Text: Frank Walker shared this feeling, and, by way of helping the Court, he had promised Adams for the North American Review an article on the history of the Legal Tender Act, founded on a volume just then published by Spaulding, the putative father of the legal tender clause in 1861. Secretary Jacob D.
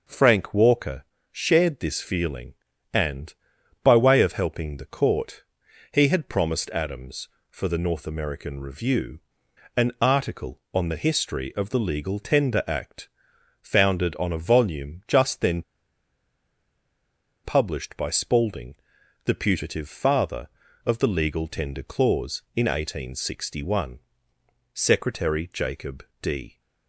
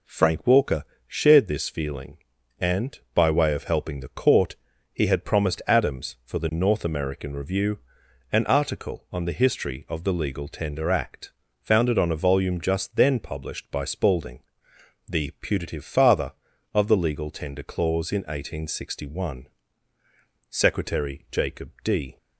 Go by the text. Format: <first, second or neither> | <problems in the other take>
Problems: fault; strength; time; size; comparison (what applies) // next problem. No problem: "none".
second | pauses between "Walker" and "shared"; slight; at 1.0 s; 0.28 s long; slight in the second // pauses between "Review" and "an"; noticeable; at 9.1 s; 0.56 s long; noticeable in the second // pauses between "then" and "published"; strong; at 15.6 s; 1.8 s long // pauses between "Jacob" and "D"; slight; at 26.0 s; 0.16 s long